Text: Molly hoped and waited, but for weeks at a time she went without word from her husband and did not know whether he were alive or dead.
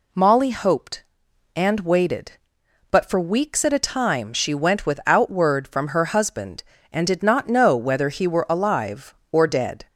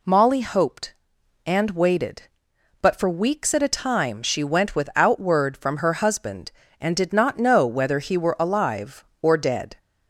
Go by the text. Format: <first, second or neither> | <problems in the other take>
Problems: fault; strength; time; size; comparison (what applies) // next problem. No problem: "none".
neither | none